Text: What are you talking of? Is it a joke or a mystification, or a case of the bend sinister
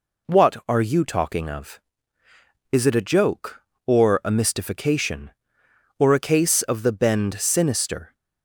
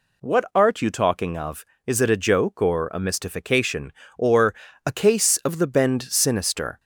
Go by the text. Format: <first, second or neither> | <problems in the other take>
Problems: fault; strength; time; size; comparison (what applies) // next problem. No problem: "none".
first | says "art" for "are"; at 0.5 s // pauses between "or" and "a"; slight; at 4.5 s; 0.32 s long